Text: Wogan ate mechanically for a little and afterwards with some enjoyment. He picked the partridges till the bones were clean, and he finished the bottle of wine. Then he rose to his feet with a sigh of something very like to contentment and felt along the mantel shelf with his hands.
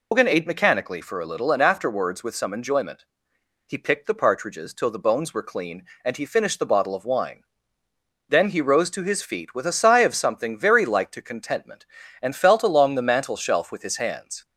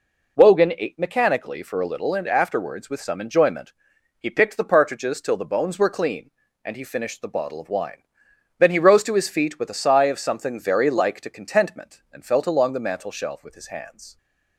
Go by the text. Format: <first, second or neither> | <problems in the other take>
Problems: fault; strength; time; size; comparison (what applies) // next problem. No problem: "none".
second | loses the start of "Wogan"; at 0.1 s; 145 ms